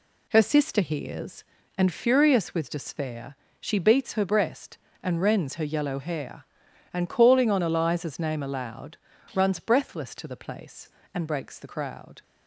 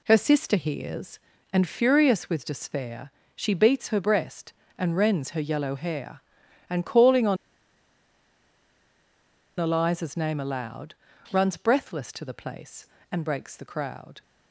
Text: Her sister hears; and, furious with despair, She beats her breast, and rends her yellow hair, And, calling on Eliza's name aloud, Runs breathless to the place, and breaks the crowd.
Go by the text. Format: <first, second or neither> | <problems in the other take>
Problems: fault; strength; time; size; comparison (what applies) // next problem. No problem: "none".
first | pauses between "on" and "Eliza's"; strong; at 7.3 s; 2.2 s long